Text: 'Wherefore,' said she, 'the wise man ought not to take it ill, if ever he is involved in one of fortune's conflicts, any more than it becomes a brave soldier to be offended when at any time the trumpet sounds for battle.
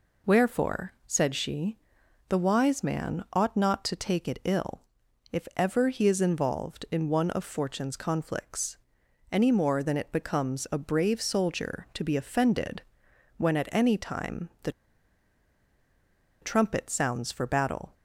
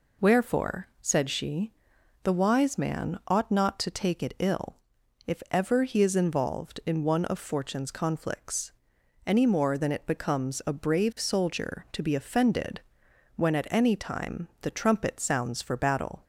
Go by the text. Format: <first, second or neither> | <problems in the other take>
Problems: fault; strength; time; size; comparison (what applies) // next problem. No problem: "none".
second | pauses between "offended" and "when"; noticeable; at 12.8 s; 0.56 s long; noticeable in the second // pauses between "the" and "trumpet"; strong; at 14.7 s; 1.7 s long